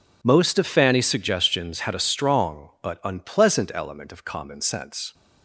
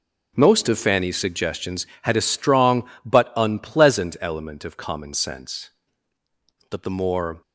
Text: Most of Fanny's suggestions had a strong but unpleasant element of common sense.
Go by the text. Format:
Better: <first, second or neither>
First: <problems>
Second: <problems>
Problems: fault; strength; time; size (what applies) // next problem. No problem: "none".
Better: first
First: none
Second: goes on to say "But the more"; noticeable; from 6.6 s on; 0.72 s long